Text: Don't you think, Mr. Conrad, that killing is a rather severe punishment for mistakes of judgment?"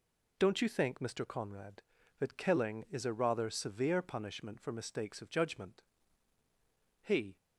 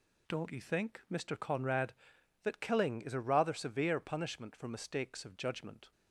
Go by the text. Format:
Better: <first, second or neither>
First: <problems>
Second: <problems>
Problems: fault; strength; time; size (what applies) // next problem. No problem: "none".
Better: second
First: goes on to say "He"; slight; from 7.0 s on; 0.34 s long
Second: none